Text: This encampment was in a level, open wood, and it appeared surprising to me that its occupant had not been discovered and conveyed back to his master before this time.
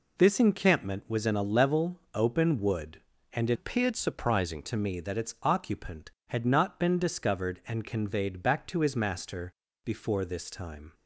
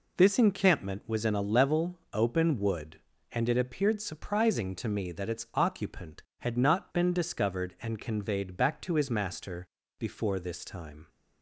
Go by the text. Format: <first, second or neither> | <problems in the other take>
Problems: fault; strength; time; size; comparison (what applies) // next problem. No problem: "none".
second | changes voice from "appeared" to "surprising"; from 3.5 to 4.6 s; 1.1 s long // pauses between "master" and "before"; slight; at 9.4 s; 0.36 s long; slight in the second